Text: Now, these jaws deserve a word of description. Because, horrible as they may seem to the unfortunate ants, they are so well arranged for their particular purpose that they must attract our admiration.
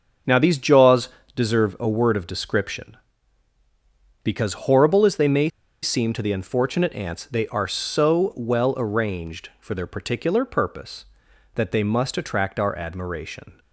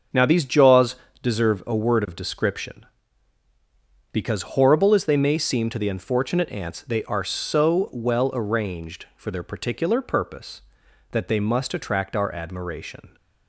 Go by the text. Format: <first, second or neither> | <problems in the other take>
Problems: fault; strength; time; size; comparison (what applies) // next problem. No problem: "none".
second | starts louder than the rest; strong; until 1.5 s; 7 dB; strong in the second // pauses between "jaws" and "deserve"; slight; at 1.0 s; 0.26 s long; slight in the second // pauses between "may" and "seem"; slight; at 5.4 s; 0.34 s long